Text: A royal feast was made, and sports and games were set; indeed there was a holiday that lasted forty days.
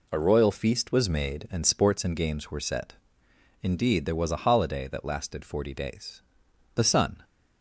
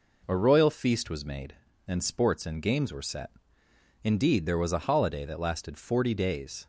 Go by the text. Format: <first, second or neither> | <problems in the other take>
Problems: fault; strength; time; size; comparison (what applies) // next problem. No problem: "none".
second | goes on to say "The Sun"; slight; from 6.7 s on; 0.46 s long